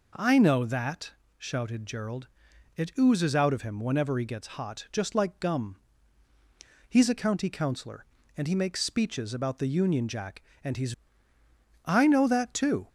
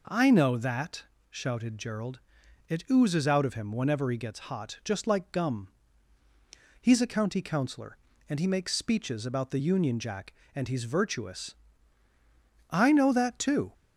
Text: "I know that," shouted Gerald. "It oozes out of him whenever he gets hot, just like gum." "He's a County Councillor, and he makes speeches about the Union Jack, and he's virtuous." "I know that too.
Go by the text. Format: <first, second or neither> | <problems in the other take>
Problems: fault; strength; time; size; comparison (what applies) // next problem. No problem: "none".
second | skips "virtuous"; at 11.3 s